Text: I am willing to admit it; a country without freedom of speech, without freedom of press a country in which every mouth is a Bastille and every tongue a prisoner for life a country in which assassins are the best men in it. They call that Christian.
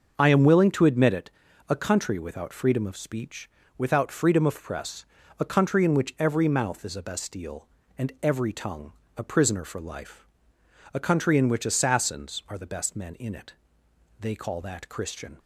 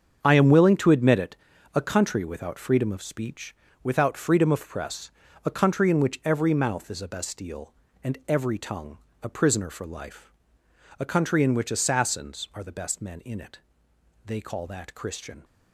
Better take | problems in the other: first | gets quieter; strong; throughout; 11 dB // starts louder than the rest; strong; until 1.2 s; 7.5 dB; also in the first // pauses between "press" and "a"; slight; at 5.1 s; 0.36 s long; slight in the first // pauses between "tongue" and "a"; slight; at 8.9 s; 0.24 s long; slight in the first // pauses between "life" and "a"; noticeable; at 10.3 s; 0.68 s long; noticeable in the first

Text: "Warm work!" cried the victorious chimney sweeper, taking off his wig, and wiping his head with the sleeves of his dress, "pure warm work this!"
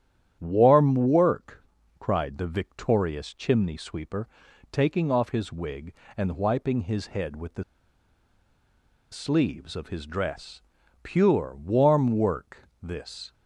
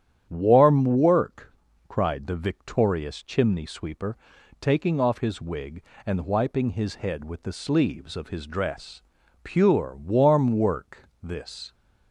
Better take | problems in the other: second | starts louder than the rest; strong; until 1.4 s; 10 dB; strong in the second // pauses between "the" and "sleeves"; strong; at 7.6 s; 1.4 s long

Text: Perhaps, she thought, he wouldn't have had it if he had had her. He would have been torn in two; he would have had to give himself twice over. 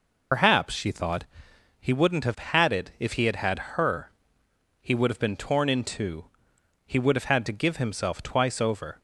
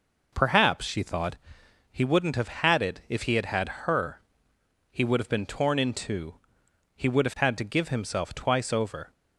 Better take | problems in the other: second | loses the start of "Perhaps"; at 0.3 s; 95 ms

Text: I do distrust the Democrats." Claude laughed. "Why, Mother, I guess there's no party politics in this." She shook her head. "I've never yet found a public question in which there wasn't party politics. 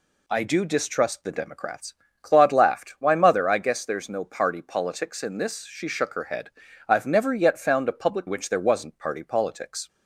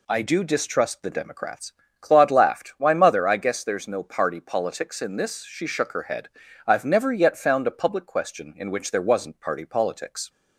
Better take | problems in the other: second | skips "question in"; at 8.2 s

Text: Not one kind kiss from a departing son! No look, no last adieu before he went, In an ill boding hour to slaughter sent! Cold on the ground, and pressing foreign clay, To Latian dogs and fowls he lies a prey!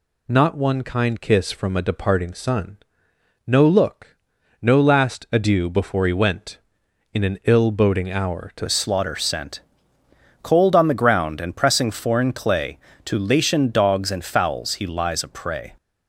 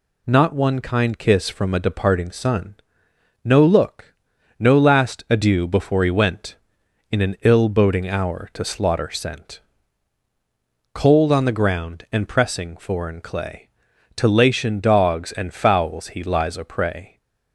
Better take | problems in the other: second | changes voice at "slaughter"; from 8.6 s on; 7.1 s long

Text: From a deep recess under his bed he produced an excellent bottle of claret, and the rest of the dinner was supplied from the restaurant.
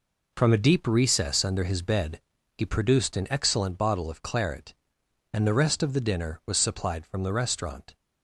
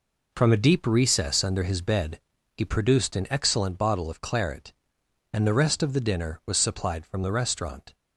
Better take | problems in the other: neither | pauses between "bed" and "he"; the same in both

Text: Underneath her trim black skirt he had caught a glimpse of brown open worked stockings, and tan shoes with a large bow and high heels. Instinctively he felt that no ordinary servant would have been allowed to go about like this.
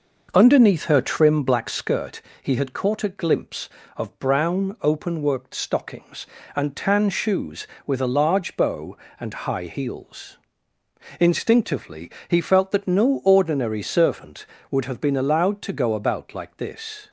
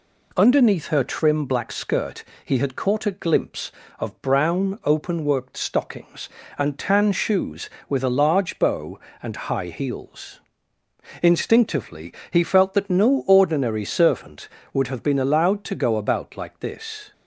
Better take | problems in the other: second | starts louder than the rest; noticeable; until 1.9 s; 5.5 dB // pauses between "skirt" and "he"; slight; at 2.2 s; 0.20 s long; slight in the second // pauses between "Instinctively" and "he"; slight; at 12.1 s; 0.16 s long; slight in the second

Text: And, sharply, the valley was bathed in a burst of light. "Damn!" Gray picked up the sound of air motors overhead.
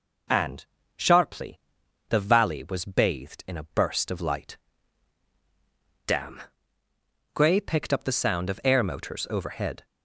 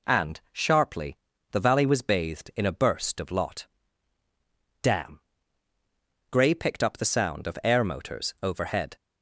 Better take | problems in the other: first | says "lot" for "light"; at 3.3 s

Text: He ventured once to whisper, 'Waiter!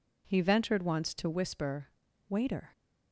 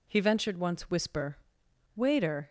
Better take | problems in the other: first | skips "to"; at 0.8 s

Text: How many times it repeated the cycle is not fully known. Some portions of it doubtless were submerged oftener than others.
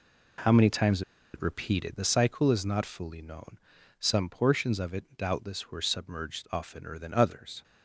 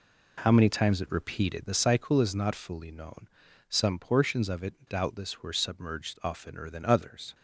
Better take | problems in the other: second | pauses between "times" and "it"; slight; at 1.0 s; 0.32 s long

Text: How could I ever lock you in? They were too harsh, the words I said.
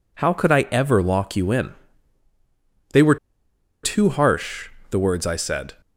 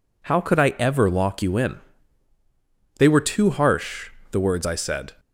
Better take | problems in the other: second | pauses between "were" and "too"; noticeable; at 3.1 s; 0.66 s long

